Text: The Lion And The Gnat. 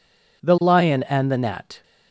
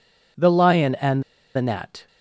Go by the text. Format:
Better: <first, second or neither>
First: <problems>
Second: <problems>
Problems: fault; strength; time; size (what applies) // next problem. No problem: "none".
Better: first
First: none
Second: pauses between "And" and "The"; slight; at 1.2 s; 0.33 s long